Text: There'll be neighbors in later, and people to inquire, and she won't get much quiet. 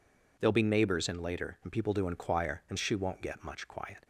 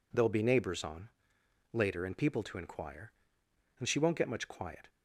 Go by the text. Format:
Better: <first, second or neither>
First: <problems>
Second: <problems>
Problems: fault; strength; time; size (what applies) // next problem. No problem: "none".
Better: first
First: none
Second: says "on" for "in"; at 0.8 s